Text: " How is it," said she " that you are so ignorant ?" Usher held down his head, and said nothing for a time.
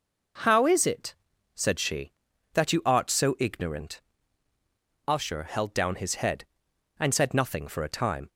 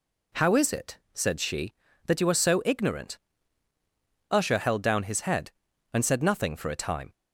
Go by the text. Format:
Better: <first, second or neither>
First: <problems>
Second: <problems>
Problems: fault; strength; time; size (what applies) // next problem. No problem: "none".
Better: second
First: says "art" for "are"; at 2.8 s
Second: none